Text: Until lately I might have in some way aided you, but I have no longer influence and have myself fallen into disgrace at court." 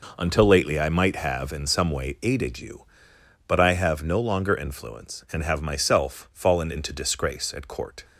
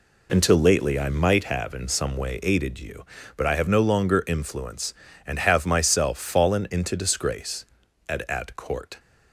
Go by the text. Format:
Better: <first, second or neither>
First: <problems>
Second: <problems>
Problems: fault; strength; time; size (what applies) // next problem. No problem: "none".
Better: first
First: none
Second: says "at" twice; at 8.2 s